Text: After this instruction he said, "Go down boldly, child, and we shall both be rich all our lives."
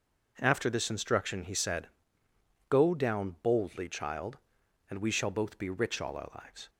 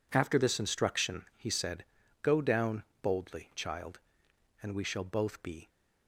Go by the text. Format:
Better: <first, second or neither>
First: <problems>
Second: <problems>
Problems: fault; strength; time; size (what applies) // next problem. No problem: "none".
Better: first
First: none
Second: pauses between "down" and "boldly"; slight; at 2.8 s; 0.18 s long // stops before "rich all our lives"; at 5.6 s